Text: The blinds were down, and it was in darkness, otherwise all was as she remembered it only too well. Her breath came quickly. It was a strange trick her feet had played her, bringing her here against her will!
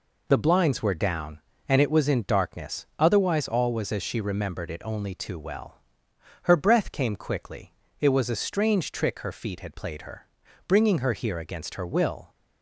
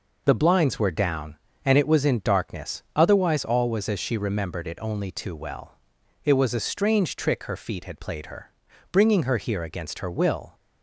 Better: first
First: none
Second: skips "Her breath came quickly"; at 6.0 s

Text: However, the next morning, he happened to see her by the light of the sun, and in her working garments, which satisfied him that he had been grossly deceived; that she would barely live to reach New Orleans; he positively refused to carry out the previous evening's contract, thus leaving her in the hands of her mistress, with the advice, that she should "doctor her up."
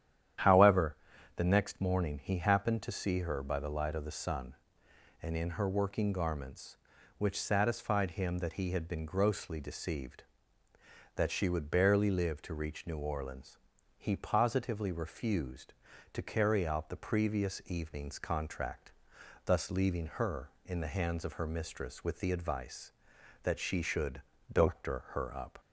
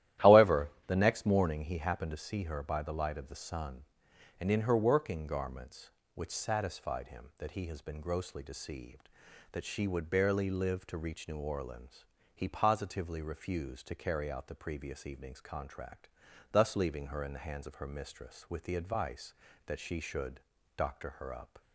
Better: first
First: starts louder than the rest; strong; until 1.8 s; 10 dB // pauses between "should" and "doctor"; slight; at 24.2 s; 0.32 s long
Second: starts louder than the rest; strong; until 1.4 s; 13.5 dB // says "has" for "had"; at 7.6 s // pauses between "should" and "doctor"; slight; at 20.4 s; 0.34 s long

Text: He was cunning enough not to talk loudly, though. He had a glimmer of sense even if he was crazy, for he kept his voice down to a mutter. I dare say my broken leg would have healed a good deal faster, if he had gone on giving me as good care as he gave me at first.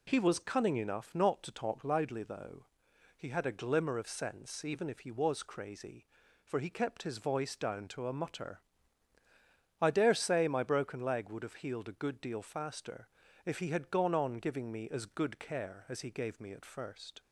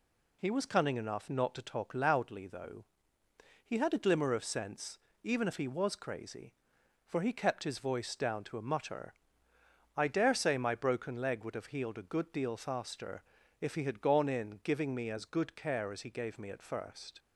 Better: first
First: none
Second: pauses between "sense" and "even"; slight; at 4.9 s; 0.26 s long // says "in" for "on"; at 14.2 s

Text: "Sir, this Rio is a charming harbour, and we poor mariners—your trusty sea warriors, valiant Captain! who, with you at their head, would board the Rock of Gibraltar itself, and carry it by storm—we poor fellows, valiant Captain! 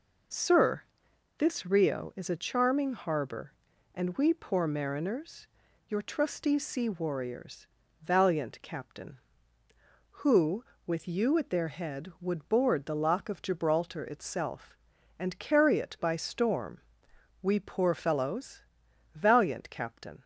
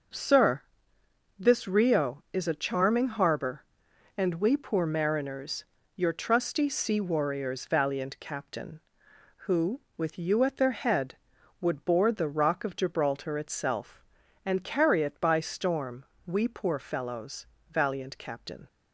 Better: second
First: says "Lock" for "Rock"; at 12.9 s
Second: none

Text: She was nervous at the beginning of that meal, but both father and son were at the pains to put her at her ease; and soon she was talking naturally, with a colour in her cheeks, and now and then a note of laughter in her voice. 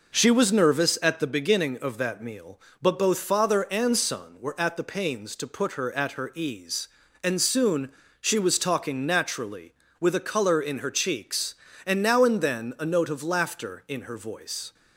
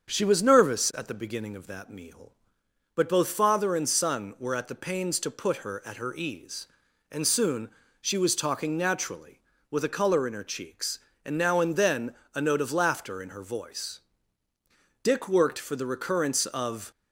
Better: first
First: pauses between "soon" and "she"; slight; at 7.9 s; 0.26 s long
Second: starts louder than the rest; strong; until 1.1 s; 7 dB // pauses between "soon" and "she"; slight; at 7.6 s; 0.32 s long // pauses between "then" and "a"; slight; at 12.1 s; 0.22 s long // goes on to say "Dick worked for the recurrence of"; strong; from 15.0 s on; 1.8 s long

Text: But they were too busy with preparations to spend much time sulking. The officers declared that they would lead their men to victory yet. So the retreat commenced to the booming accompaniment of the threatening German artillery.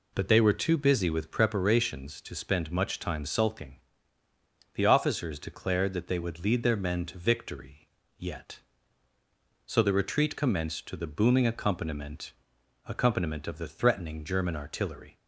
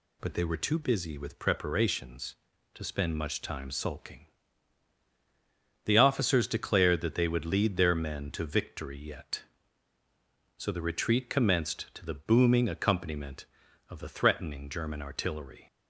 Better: second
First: pauses between "victory" and "yet"; slight; at 7.8 s; 0.30 s long // says "accompaniment" twice; at 12.8 s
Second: none

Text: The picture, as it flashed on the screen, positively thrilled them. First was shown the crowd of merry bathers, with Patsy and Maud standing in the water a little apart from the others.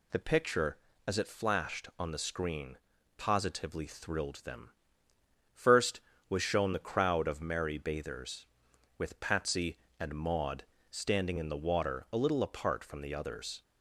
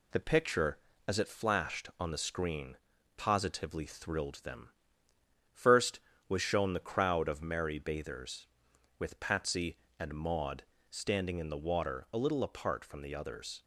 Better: first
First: pauses between "Maud" and "standing"; slight; at 10.6 s; 0.26 s long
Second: gets quieter; slight; throughout; 3 dB // pauses between "Maud" and "standing"; slight; at 10.6 s; 0.26 s long

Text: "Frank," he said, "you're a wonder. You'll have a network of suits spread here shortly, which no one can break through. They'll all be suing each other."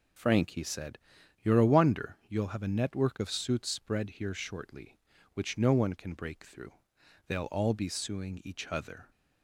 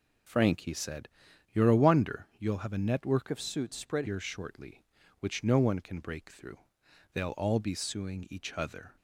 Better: first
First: none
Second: changes voice from "of" to "spread"; from 3.2 to 4.0 s; 0.8 s long

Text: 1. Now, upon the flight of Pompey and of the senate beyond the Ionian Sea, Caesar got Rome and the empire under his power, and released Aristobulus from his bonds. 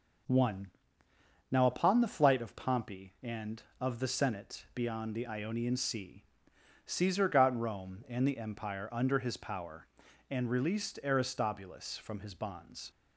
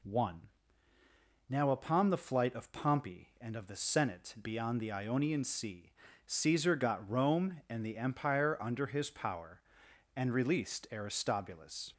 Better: first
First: none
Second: stops before "from his bonds"; at 11.9 s

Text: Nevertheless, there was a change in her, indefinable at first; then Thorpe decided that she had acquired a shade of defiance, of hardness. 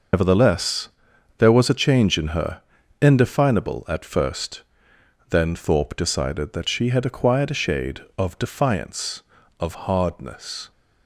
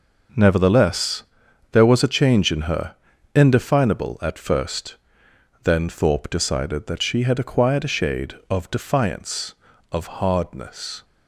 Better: second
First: loses the start of "Nevertheless"; at 0.1 s; 165 ms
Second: none

